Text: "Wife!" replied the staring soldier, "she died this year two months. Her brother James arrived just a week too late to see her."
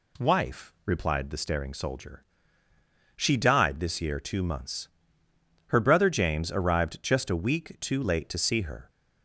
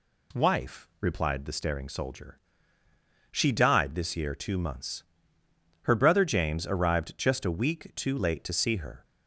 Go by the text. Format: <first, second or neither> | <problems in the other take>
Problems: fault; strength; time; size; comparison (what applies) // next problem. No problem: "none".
neither | none